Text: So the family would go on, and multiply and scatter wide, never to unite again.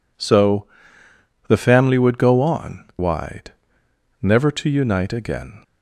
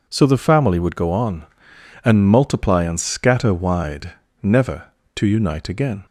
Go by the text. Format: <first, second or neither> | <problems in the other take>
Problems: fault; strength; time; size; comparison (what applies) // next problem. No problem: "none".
second | pauses between "So" and "the"; noticeable; at 0.6 s; 0.80 s long // skips "and multiply and scatter"; at 2.9 s